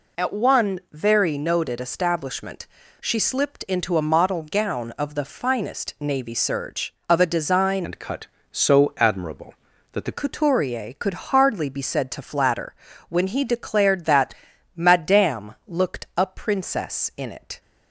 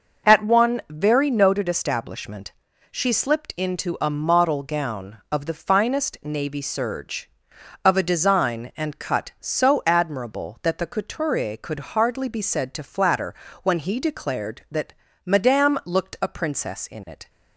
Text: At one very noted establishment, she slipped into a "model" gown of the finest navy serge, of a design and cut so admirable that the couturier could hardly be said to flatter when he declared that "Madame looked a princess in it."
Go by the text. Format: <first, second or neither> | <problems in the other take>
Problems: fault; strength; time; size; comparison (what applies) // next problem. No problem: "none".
second | changes voice from "and" to "the"; from 7.8 to 10.1 s; 2.3 s long // pauses between "flatter" and "when"; slight; at 12.7 s; 0.34 s long; slight in the second // pauses between "that" and "Madame"; at 14.3 s; 0.40 s long; slight in the second